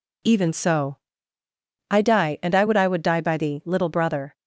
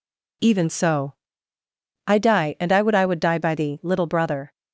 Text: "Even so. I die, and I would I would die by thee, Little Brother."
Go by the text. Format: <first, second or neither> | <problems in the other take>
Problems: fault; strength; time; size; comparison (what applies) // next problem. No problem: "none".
neither | none